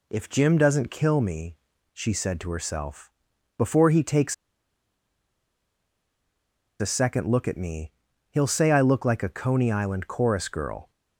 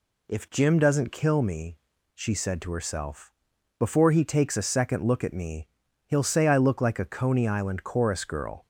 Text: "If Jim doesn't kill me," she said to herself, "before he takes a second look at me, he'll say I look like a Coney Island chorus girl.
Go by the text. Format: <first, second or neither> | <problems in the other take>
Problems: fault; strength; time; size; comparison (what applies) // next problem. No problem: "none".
second | pauses between "takes" and "a"; strong; at 4.3 s; 2.4 s long